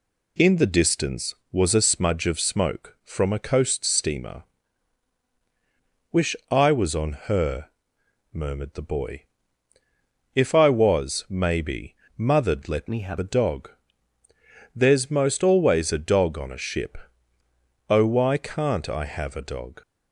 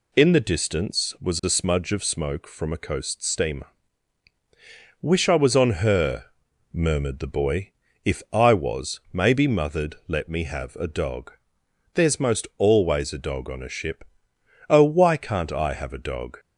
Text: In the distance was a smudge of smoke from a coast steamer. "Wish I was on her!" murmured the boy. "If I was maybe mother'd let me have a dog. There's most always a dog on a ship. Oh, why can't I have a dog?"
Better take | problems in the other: second | pauses between "Wish" and "I"; slight; at 6.3 s; 0.16 s long // pauses between "maybe" and "mother'd"; slight; at 11.9 s; 0.24 s long // changes voice from "me" to "have"; from 12.8 to 13.1 s; 0.3 s long

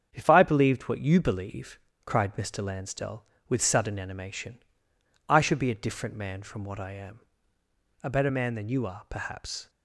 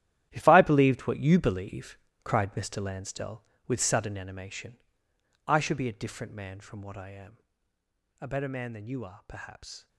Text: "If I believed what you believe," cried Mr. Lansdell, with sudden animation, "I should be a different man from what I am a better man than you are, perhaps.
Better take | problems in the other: first | gets quieter; strong; throughout; 12.5 dB // starts louder than the rest; strong; until 1.3 s; 12.5 dB; strong in the first // pauses between "am" and "a"; noticeable; at 7.3 s; 0.82 s long; noticeable in the first

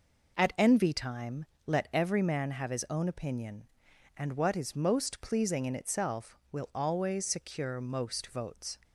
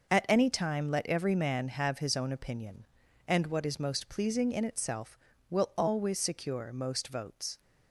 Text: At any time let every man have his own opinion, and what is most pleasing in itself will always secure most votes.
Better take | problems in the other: second | says "envy" for "any"; at 0.5 s // pauses between "time" and "let"; slight; at 1.4 s; 0.22 s long

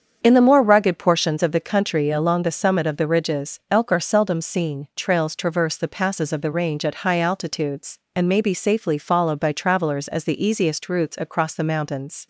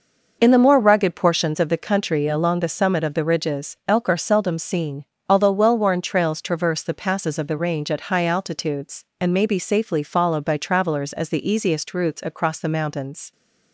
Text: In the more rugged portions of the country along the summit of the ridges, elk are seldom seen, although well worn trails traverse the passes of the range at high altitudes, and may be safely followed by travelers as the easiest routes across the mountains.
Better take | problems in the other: second | starts louder than the rest; strong; until 1.2 s; 7.5 dB // skips "although well worn"; at 4.9 s

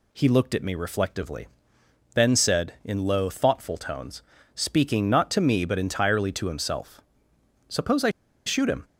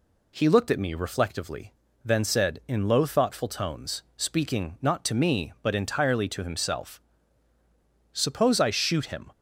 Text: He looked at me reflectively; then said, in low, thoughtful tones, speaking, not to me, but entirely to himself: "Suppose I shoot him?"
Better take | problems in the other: second | pauses between "I" and "shoot"; at 8.0 s; 0.37 s long

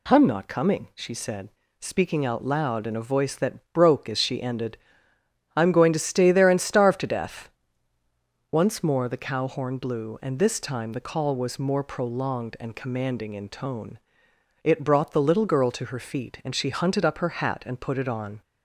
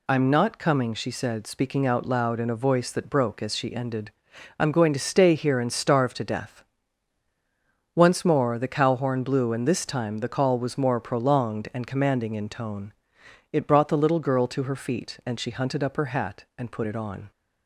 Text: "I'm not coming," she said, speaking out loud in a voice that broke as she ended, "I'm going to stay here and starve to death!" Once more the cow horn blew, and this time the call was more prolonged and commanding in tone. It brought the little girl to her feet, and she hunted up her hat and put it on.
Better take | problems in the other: second | says "there" for "here"; at 6.3 s

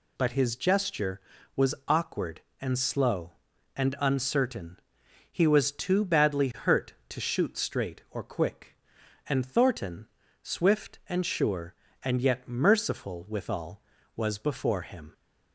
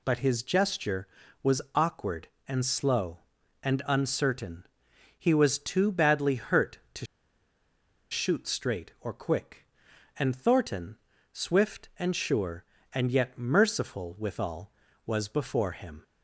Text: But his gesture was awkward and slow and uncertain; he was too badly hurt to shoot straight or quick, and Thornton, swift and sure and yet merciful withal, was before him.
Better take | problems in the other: first | pauses between "to" and "shoot"; at 7.0 s; 1.0 s long

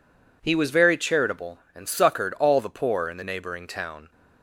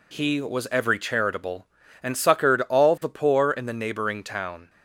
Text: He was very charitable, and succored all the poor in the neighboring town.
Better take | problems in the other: first | says "every" for "very"; at 0.6 s

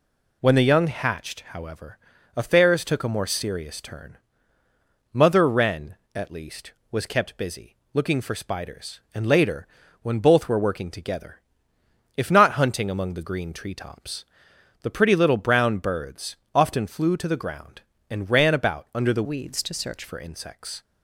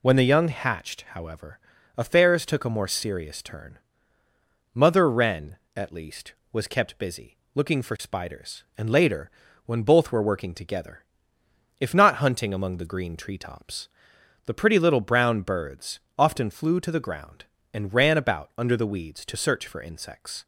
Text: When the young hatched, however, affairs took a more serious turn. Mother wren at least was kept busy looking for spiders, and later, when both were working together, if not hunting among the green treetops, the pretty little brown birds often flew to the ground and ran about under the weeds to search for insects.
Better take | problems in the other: second | pauses between "busy" and "looking"; slight; at 7.7 s; 0.20 s long; slight in the second // pauses between "birds" and "often"; slight; at 16.3 s; 0.18 s long; slight in the second // changes voice from "weeds" to "search"; from 19.2 to 20.0 s; 0.8 s long

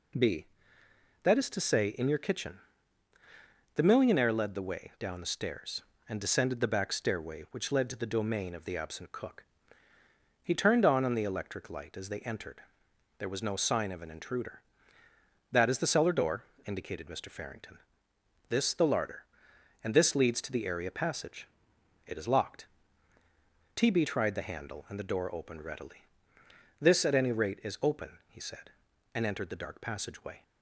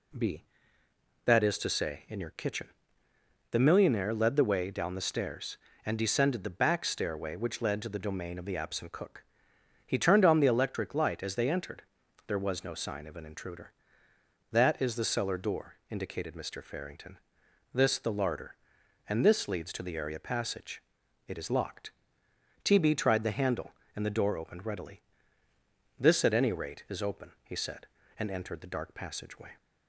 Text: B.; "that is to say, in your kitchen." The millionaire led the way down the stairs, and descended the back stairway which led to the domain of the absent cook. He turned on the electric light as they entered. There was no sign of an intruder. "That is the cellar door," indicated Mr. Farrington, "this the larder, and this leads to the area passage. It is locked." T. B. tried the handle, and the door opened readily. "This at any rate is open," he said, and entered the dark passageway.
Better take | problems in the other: second | says "on" twice; at 11.0 s

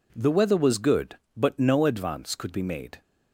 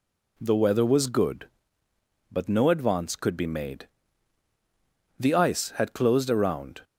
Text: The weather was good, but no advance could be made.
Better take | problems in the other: first | goes on to say "The ice had closed around"; from 5.1 s on; 1.6 s long

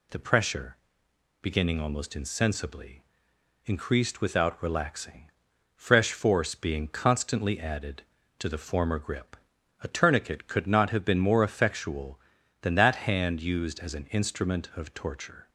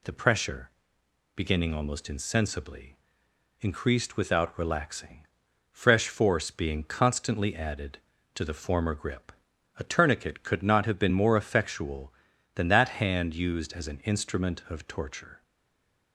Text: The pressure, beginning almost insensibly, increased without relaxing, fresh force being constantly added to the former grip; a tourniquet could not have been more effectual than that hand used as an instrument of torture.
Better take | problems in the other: first | stays silent after the last word; slight; from 15.4 s on; 0.7 s long

